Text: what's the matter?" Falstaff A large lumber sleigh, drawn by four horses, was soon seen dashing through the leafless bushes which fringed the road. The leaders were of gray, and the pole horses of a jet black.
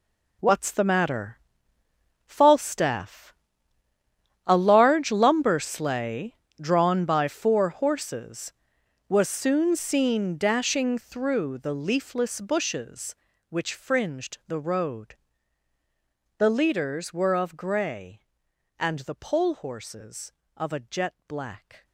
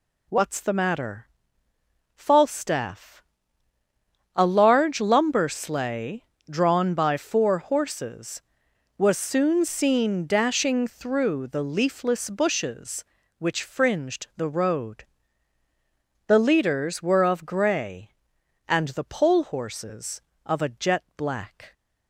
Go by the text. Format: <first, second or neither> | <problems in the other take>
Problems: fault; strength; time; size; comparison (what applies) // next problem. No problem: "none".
second | gets quieter; strong; throughout; 13 dB // pauses between "Falstaff" and "A"; at 3.3 s; 1.1 s long; also in the second